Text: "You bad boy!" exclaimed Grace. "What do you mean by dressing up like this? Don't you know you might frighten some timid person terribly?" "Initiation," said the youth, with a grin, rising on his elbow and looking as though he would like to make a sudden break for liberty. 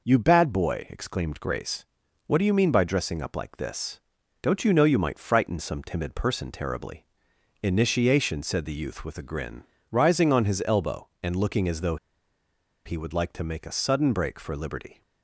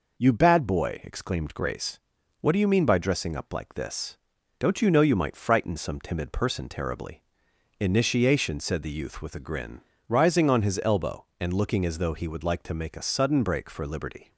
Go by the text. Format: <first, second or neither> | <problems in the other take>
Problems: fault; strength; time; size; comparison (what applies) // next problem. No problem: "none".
second | pauses between "though" and "he"; noticeable; at 11.9 s; 0.89 s long